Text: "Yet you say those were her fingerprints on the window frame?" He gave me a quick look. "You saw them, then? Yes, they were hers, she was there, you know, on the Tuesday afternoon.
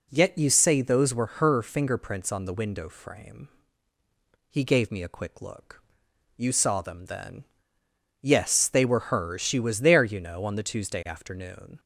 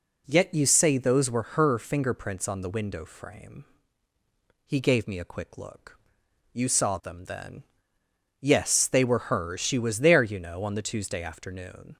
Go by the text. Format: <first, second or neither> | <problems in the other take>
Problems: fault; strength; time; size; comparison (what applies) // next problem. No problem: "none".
neither | none